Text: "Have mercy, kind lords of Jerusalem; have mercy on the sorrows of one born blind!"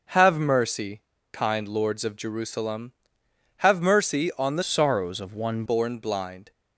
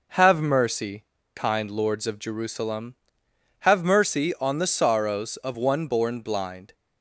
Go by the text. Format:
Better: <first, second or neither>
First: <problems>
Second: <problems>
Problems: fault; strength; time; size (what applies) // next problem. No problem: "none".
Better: second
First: changes voice from "sorrows" to "one"; from 4.6 to 5.6 s; 1.0 s long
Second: none